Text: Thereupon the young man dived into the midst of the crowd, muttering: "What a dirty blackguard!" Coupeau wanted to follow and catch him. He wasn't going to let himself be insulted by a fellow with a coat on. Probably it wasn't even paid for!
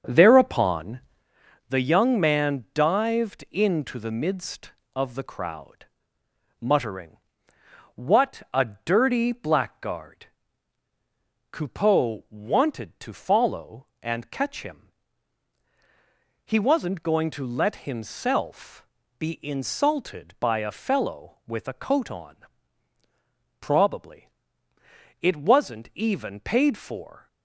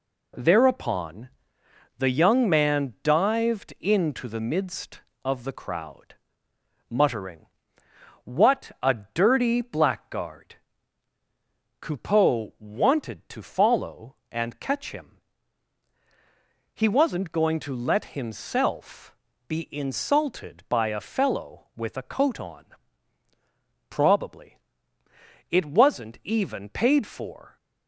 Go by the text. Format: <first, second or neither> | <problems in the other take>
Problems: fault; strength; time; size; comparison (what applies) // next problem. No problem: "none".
second | starts louder than the rest; until 1.3 s; 6.5 dB // pauses between "Thereupon" and "the"; noticeable; at 0.9 s; 0.70 s long; noticeable in the second // pauses between "himself" and "be"; slight; at 18.8 s; 0.32 s long; slight in the second // pauses between "Probably" and "it"; noticeable; at 24.2 s; 0.90 s long; noticeable in the second